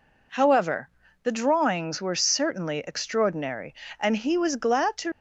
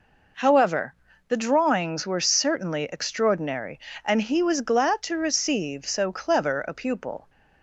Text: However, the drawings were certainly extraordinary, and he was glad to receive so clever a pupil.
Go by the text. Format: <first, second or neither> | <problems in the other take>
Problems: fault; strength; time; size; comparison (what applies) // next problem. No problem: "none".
second | stops before "receive so clever a pupil"; at 5.1 s